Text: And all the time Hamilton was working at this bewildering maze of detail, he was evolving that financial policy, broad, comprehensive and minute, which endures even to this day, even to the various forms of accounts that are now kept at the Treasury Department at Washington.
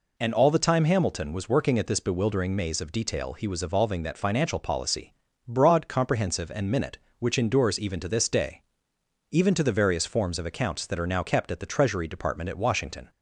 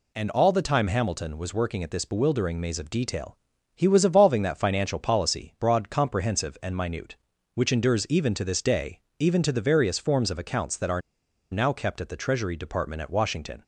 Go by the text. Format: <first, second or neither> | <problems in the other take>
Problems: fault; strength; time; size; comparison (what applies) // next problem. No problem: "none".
first | pauses between "are" and "now"; noticeable; at 11.0 s; 0.50 s long